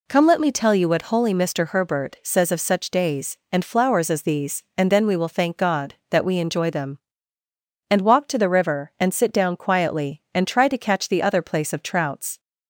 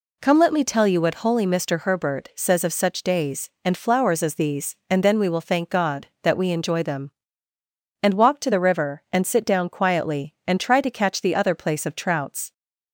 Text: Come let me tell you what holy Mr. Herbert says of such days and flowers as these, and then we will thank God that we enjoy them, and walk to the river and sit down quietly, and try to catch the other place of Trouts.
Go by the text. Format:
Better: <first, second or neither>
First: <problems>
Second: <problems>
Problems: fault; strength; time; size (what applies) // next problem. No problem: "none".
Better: neither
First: none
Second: none